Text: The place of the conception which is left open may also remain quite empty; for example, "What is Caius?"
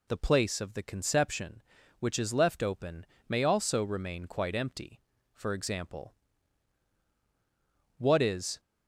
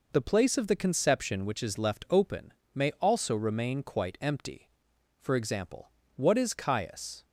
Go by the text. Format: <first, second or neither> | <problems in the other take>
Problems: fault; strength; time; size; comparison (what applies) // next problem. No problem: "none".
second | pauses between "open" and "may"; slight; at 3.0 s; 0.24 s long; slight in the second // stops before "Caius"; at 8.5 s